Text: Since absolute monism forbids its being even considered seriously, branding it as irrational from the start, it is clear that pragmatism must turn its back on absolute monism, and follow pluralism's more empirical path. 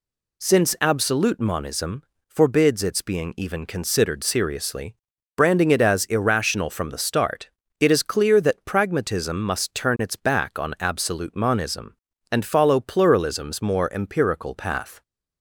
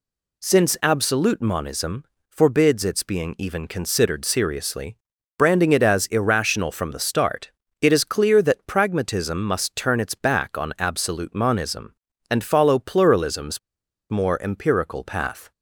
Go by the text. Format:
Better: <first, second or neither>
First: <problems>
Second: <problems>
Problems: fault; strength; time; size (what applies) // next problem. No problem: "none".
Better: first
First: pauses between "monism" and "forbids"; slight; at 2.0 s; 0.24 s long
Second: pauses between "monism" and "forbids"; slight; at 2.0 s; 0.24 s long // pauses between "pluralism's" and "more"; noticeable; at 13.5 s; 0.51 s long